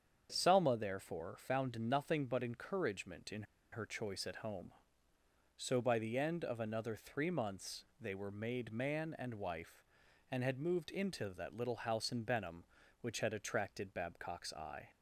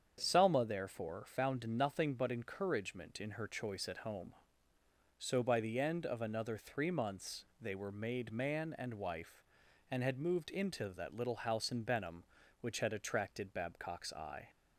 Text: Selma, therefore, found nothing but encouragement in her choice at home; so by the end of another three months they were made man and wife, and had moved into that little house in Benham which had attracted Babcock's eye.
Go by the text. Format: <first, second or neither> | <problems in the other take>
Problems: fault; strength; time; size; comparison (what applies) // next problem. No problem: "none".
second | starts louder than the rest; strong; until 1.3 s; 7.5 dB; strong in the second // pauses between "in" and "her"; slight; at 3.4 s; 0.29 s long // pauses between "months" and "they"; slight; at 7.8 s; 0.16 s long; slight in the second